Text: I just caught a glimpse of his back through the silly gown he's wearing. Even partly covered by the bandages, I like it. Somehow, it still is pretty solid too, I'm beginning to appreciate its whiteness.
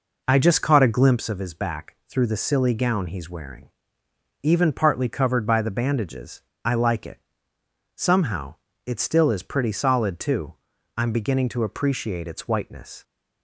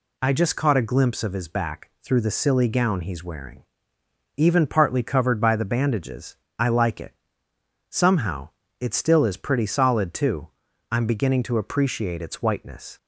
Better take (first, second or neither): second